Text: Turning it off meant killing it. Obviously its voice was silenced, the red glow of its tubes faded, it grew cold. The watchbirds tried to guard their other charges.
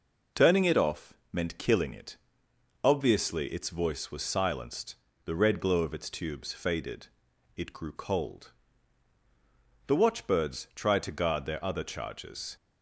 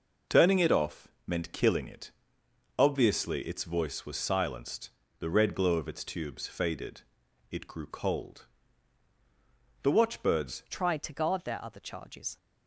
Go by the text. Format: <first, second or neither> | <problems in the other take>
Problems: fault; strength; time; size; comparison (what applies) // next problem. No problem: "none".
first | pauses between "off" and "meant"; slight; at 1.0 s; 0.18 s long; slight in the first // changes voice at "tried"; from 10.7 s on; 1.6 s long